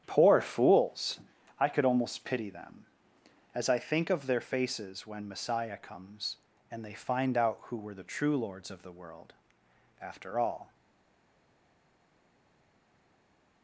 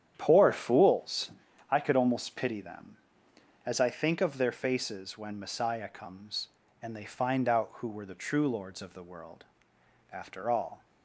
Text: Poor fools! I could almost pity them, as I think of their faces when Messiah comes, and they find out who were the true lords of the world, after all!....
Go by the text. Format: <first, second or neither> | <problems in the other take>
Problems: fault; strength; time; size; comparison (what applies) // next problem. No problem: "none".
second | starts louder than the rest; strong; until 1.0 s; 9.5 dB; strong in the second // stays silent after the last word; strong; from 10.7 s on; 2.9 s long